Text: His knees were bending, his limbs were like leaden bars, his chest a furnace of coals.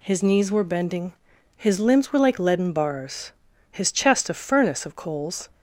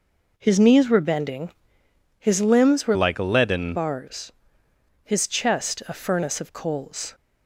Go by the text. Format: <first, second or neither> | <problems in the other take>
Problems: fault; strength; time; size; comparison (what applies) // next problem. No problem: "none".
first | changes voice from "like" to "leaden"; from 2.9 to 3.7 s; 0.8 s long